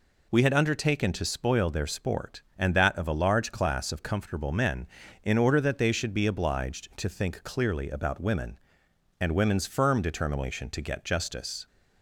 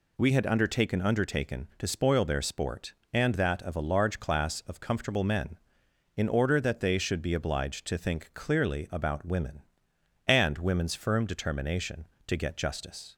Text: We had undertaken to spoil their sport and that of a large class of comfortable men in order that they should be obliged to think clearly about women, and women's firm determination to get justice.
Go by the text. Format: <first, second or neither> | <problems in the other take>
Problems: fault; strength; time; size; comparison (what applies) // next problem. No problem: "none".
first | says "undertaken" twice; at 1.0 s